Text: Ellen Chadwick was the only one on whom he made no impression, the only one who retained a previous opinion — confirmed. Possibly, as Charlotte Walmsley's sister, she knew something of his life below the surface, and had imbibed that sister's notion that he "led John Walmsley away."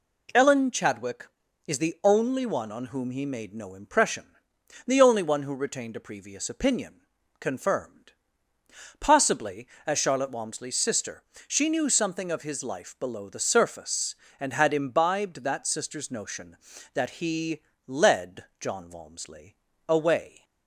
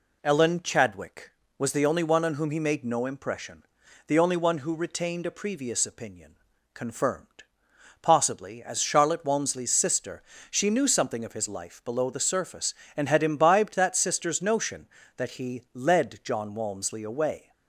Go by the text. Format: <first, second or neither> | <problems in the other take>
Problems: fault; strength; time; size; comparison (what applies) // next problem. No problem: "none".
second | says "is" for "was"; at 1.6 s // pauses between "he" and "led"; slight; at 17.6 s; 0.26 s long // pauses between "led" and "John"; slight; at 18.4 s; 0.16 s long // pauses between "Walmsley" and "away"; slight; at 19.5 s; 0.32 s long